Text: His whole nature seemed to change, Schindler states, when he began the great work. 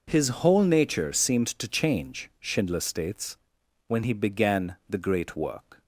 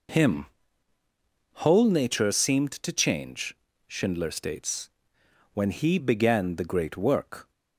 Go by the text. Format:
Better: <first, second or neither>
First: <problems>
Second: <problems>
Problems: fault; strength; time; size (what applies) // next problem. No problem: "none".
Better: first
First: none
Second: says "Him" for "His"; at 0.0 s